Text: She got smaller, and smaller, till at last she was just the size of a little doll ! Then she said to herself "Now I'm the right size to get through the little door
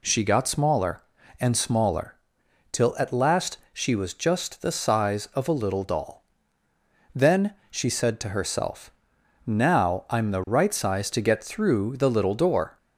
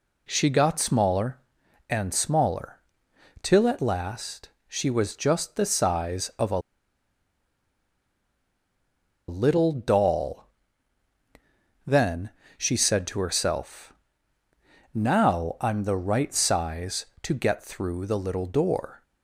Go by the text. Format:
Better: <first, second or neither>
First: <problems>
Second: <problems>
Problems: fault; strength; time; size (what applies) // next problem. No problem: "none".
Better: first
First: pauses between "last" and "she"; slight; at 3.5 s; 0.16 s long // pauses between "Then" and "she"; slight; at 7.5 s; 0.16 s long // pauses between "herself" and "Now"; noticeable; at 8.9 s; 0.54 s long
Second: pauses between "last" and "she"; slight; at 4.4 s; 0.18 s long // pauses between "a" and "little"; strong; at 6.5 s; 2.6 s long // pauses between "Then" and "she"; slight; at 12.3 s; 0.26 s long // pauses between "herself" and "Now"; at 13.9 s; 1.0 s long